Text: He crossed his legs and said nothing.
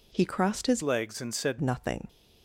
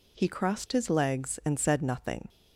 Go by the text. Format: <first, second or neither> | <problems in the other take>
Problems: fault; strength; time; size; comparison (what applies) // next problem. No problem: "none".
second | changes voice from "legs" to "said"; from 0.8 to 1.5 s; 0.7 s long